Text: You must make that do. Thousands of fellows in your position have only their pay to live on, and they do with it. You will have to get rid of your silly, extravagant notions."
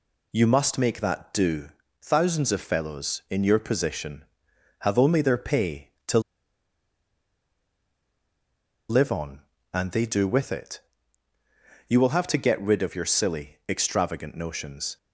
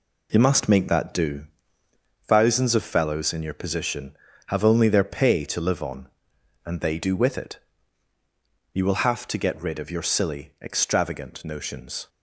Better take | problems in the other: second | pauses between "to" and "live"; strong; at 6.1 s; 2.6 s long

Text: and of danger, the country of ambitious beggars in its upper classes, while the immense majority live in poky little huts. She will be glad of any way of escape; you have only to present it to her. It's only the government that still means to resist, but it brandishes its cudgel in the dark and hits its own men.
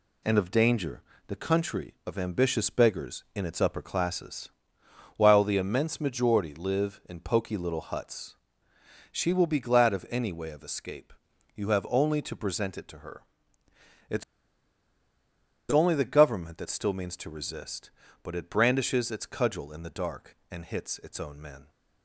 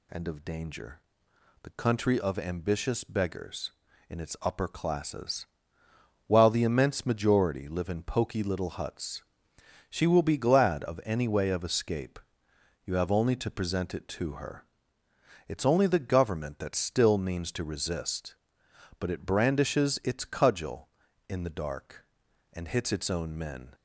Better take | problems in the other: second | pauses between "It's" and "only"; strong; at 14.2 s; 1.4 s long

